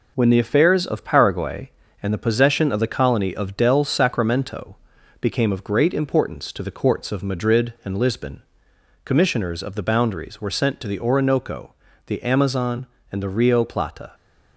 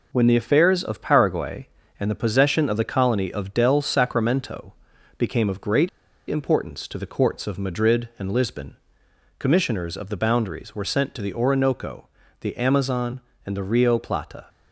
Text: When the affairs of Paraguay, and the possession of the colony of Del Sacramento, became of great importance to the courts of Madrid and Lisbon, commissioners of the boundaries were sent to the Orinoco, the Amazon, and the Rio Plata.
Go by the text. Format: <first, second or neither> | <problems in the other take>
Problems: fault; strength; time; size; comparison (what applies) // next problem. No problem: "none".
first | pauses between "great" and "importance"; at 5.8 s; 0.39 s long